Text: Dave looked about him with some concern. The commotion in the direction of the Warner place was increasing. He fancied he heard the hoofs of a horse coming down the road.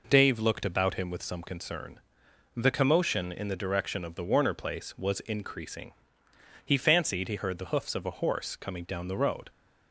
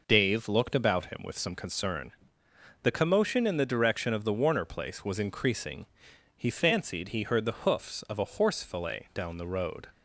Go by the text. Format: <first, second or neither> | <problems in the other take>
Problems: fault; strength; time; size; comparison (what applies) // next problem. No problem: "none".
first | says "fillet" for "coming"; at 8.6 s